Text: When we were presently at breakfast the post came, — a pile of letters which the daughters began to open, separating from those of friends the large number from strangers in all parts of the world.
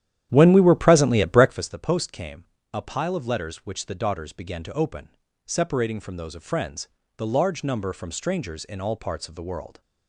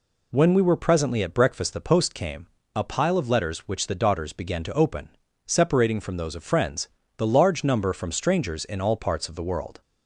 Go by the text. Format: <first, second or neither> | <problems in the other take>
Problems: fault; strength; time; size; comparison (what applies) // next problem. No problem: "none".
second | starts louder than the rest; strong; until 1.6 s; 11 dB // pauses between "friends" and "the"; slight; at 6.8 s; 0.30 s long; slight in the second